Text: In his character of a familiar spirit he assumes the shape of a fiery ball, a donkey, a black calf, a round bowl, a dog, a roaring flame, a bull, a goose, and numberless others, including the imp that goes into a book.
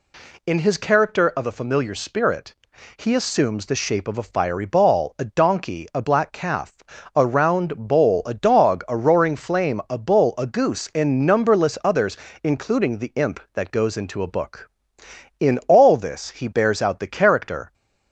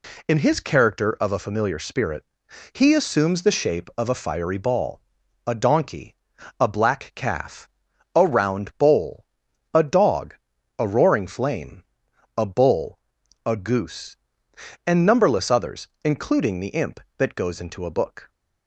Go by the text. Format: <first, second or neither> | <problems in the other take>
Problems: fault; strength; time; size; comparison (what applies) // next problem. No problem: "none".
second | pauses between "spirit" and "he"; at 2.5 s; 0.40 s long; noticeable in the second // goes on to say "In all this he bears out the character"; strong; from 15.4 s on; 2.3 s long